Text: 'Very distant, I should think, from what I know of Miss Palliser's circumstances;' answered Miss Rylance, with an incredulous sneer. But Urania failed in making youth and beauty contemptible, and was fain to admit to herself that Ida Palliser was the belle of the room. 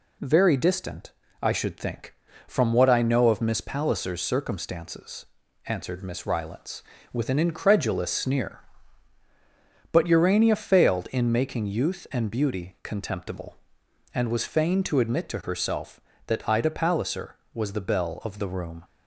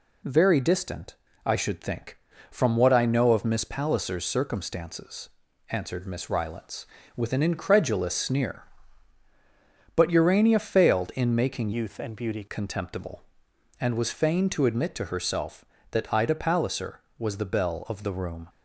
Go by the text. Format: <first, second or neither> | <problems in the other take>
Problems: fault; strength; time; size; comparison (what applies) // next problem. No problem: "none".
first | changes voice from "youth" to "beauty"; from 11.7 to 12.4 s; 0.7 s long